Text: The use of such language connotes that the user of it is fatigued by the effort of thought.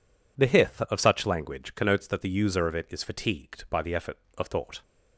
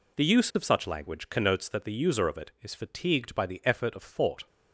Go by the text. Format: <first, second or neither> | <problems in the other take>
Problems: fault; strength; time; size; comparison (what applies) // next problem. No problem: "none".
second | says "hith" for "use"; at 0.4 s